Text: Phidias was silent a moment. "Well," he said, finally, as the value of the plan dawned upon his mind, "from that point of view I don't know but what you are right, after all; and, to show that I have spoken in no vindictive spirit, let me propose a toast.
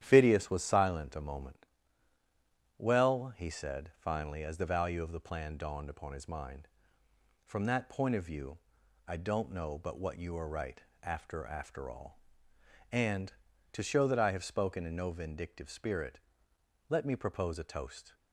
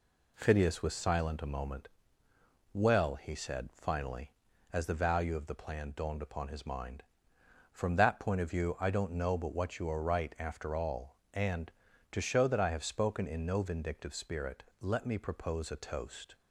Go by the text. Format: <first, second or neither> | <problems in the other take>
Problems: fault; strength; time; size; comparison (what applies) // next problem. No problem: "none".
second | starts louder than the rest; strong; until 1.0 s; 11 dB // pauses between "view" and "I"; noticeable; at 8.5 s; 0.48 s long // says "after" twice; at 11.4 s